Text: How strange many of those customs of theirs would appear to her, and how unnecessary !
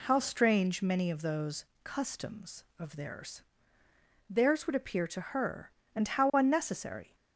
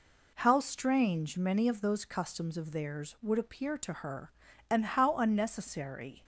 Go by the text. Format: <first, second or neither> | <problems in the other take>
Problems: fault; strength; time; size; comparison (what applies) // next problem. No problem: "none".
second | pauses between "those" and "customs"; slight; at 1.6 s; 0.18 s long // says "theirs" twice; at 4.2 s